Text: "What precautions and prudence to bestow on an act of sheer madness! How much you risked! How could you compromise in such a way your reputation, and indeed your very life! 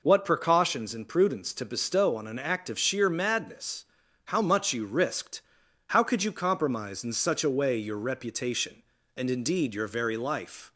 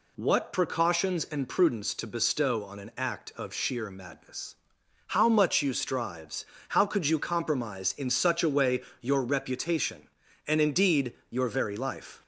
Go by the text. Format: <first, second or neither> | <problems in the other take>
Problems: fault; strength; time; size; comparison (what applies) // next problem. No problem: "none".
first | says "strives" for "risked"; at 5.7 s // pauses between "way" and "your"; slight; at 8.8 s; 0.20 s long // pauses between "indeed" and "your"; slight; at 11.1 s; 0.18 s long